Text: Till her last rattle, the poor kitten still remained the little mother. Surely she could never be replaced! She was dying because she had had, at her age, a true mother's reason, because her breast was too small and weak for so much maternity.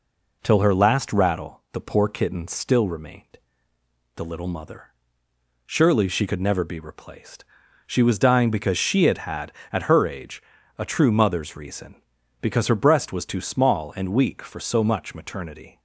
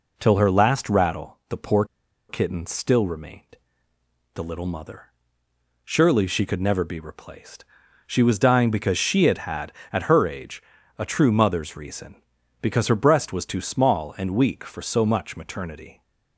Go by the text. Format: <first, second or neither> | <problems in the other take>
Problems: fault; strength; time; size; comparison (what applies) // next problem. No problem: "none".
first | pauses between "poor" and "kitten"; at 1.8 s; 0.45 s long // pauses between "remained" and "the"; noticeable; at 3.4 s; 0.92 s long; noticeable in the first